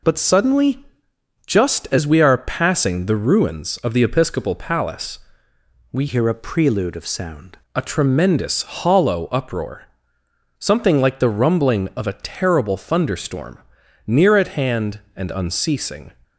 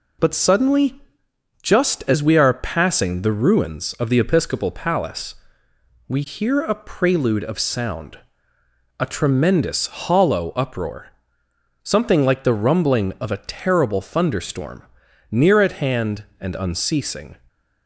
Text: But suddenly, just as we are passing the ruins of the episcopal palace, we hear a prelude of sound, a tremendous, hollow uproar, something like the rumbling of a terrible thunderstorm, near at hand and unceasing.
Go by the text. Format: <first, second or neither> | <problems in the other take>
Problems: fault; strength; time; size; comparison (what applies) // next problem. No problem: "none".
second | changes voice from "hear" to "sound"; from 6.0 to 7.5 s; 1.5 s long